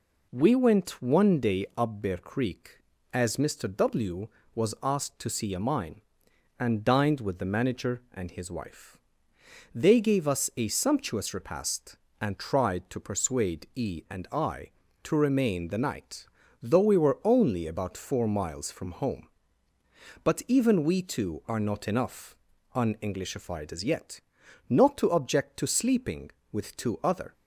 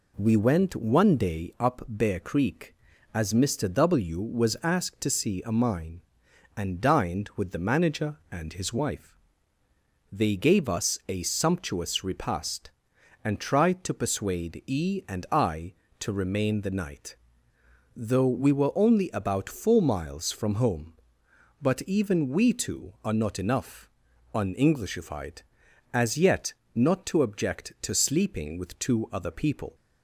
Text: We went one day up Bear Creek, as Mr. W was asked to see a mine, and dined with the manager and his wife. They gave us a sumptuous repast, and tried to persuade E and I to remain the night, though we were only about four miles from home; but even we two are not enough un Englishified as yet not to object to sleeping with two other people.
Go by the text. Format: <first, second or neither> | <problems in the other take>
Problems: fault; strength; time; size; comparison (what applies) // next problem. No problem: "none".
second | pauses between "enough" and "un"; at 22.3 s; 0.38 s long; noticeable in the second // pauses between "yet" and "not"; noticeable; at 24.2 s; 0.50 s long; slight in the second // stops before "people"; at 27.3 s